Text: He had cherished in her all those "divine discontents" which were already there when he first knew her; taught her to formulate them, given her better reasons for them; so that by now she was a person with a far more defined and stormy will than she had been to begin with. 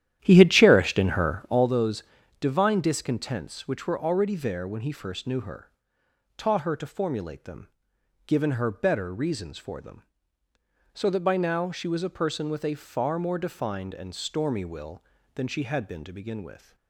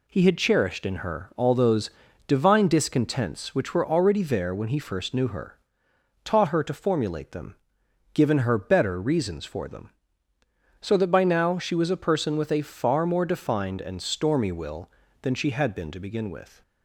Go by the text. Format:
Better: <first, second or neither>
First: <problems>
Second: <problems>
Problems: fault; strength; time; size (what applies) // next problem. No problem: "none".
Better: second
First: starts louder than the rest; strong; until 1.7 s; 11.5 dB // pauses between "those" and "divine"; at 2.0 s; 0.38 s long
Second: pauses between "those" and "divine"; at 1.8 s; 0.38 s long